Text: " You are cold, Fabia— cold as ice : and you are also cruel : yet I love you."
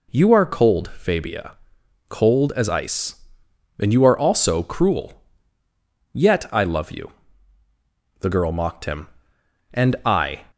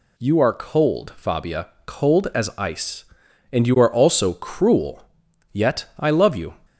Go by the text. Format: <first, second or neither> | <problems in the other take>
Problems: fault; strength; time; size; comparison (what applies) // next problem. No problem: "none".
second | goes on to say "The girl mocked him And I"; strong; from 8.1 s on; 2.2 s long